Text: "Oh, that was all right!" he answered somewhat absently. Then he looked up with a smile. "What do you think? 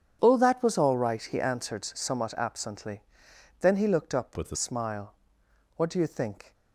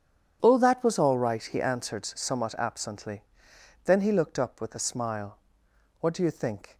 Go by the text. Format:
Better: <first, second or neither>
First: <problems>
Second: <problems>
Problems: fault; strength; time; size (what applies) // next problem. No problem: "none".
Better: second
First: starts louder than the rest; strong; until 1.2 s; 8.5 dB // changes voice from "with" to "a"; from 4.3 to 4.5 s; 0.2 s long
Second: starts louder than the rest; strong; until 1.4 s; 8.5 dB